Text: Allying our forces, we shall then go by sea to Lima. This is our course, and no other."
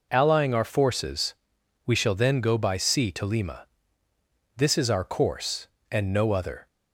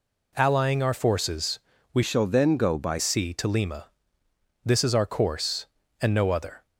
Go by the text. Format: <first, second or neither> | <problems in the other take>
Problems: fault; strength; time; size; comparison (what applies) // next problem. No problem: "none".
first | changes voice from "shall" to "by"; from 2.0 to 3.0 s; 1.0 s long